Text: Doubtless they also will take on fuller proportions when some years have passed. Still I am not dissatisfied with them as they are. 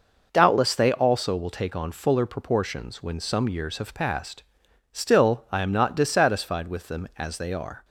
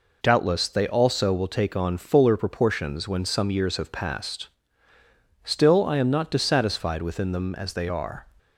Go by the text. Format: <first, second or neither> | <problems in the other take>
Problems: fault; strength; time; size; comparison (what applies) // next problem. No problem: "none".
first | says "within" for "with"; at 7.0 s